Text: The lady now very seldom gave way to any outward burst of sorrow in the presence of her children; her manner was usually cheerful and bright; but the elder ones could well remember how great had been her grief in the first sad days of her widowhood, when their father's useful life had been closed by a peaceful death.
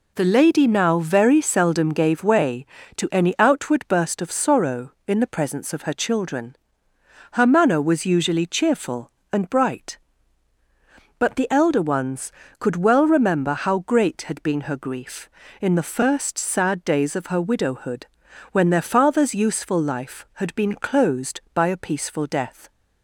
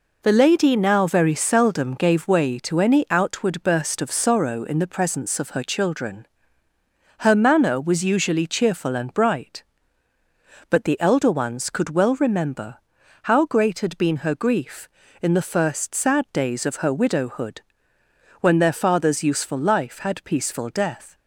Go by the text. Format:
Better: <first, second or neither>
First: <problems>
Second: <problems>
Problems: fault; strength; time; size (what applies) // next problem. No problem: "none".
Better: first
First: none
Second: pauses between "remember" and "how"; noticeable; at 12.7 s; 0.50 s long // skips "been closed by a"; at 20.2 s